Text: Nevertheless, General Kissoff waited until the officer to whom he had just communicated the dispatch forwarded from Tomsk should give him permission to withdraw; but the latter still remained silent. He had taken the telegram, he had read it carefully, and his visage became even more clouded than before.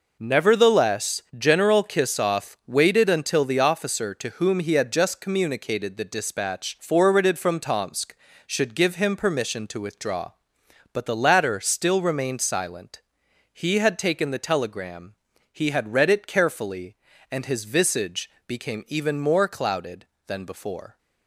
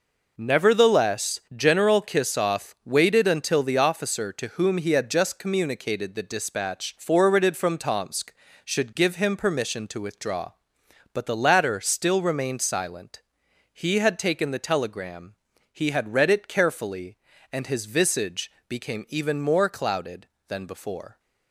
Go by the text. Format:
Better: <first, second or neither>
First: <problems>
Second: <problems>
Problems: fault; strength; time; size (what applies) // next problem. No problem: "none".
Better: neither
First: pauses between "visage" and "became"; slight; at 18.2 s; 0.20 s long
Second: pauses between "visage" and "became"; slight; at 18.4 s; 0.20 s long